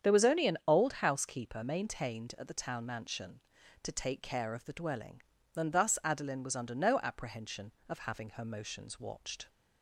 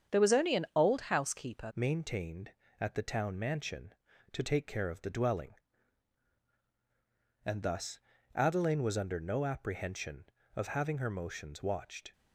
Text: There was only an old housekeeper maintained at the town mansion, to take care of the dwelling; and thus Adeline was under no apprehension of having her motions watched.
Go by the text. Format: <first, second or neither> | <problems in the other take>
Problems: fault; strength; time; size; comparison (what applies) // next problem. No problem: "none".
first | starts louder than the rest; strong; until 1.2 s; 8 dB; strong in the first // changes voice at "maintained"; from 1.7 s on; 10.4 s long // pauses between "thus" and "Adeline"; slight; at 7.9 s; 0.36 s long